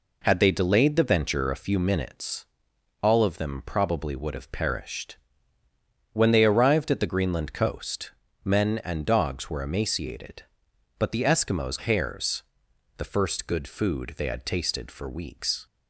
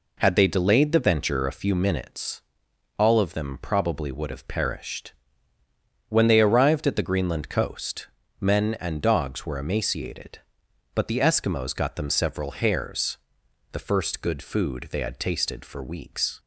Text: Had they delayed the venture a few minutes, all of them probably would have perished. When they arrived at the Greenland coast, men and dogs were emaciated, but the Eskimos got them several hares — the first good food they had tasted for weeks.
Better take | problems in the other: second | skips "got them several"; at 11.7 s

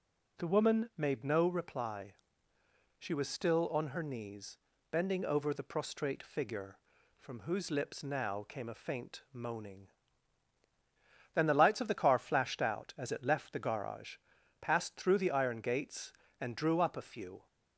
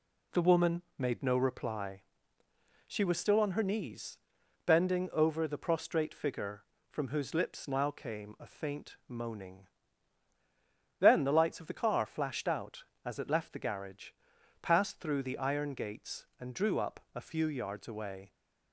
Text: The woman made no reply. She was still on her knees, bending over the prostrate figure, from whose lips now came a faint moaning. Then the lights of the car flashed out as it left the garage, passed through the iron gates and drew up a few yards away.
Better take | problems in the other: second | stops before "yards away"; at 17.4 s

